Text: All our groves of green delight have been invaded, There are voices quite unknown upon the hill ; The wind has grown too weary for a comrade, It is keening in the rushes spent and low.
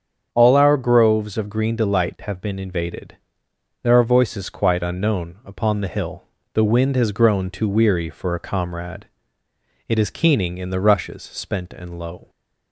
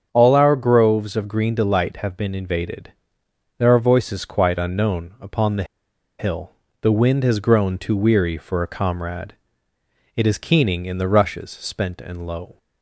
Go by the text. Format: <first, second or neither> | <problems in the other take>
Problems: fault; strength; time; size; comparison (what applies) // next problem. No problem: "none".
first | starts louder than the rest; strong; until 1.1 s; 7.5 dB; strong in the first // pauses between "the" and "hill"; noticeable; at 5.6 s; 0.55 s long